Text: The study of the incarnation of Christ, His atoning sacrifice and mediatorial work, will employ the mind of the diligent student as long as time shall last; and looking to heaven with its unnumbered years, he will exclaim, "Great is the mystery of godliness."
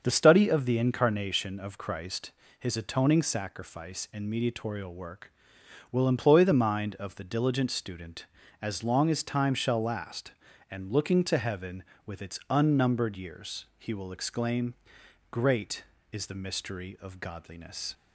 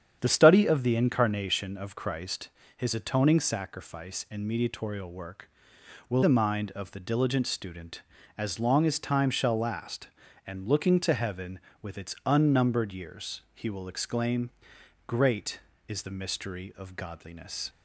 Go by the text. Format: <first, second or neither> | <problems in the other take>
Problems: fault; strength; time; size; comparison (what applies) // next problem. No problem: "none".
first | starts louder than the rest; strong; until 1.2 s; 8.5 dB; also in the first // skips "employ"; at 6.2 s